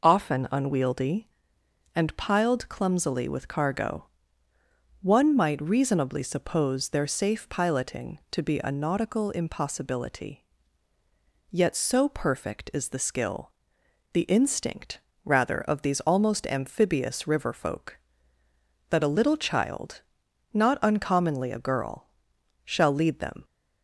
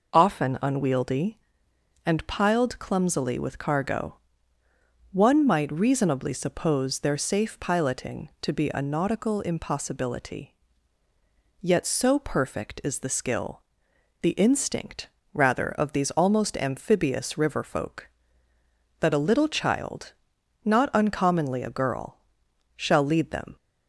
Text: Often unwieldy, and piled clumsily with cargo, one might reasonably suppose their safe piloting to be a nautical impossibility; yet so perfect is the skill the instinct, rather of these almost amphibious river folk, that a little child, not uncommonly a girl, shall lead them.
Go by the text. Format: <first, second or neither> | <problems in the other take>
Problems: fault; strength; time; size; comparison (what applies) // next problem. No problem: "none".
neither | pauses between "skill" and "the"; noticeable; the same in both